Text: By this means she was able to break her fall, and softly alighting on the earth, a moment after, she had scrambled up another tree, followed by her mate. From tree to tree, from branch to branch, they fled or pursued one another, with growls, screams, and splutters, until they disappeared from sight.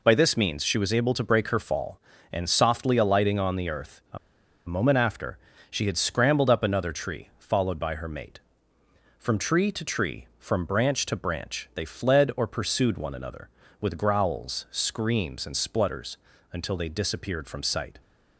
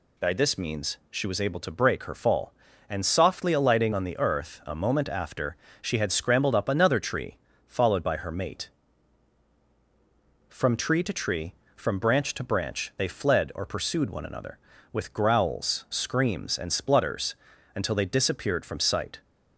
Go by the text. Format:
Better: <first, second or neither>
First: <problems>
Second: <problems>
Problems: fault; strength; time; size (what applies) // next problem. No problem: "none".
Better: second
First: pauses between "a" and "moment"; noticeable; at 4.1 s; 0.50 s long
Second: none